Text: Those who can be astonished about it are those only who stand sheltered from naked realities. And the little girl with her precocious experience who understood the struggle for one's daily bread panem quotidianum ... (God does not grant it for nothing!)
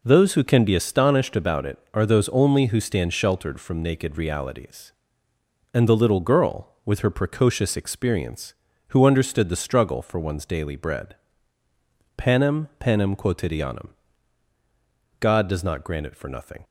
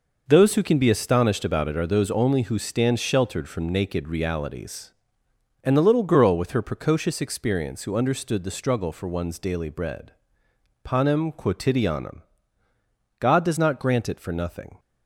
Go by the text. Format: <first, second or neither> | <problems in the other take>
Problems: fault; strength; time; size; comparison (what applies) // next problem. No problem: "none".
second | pauses between "bread" and "panem"; at 11.1 s; 1.0 s long; noticeable in the second // says "panem" twice; at 12.7 s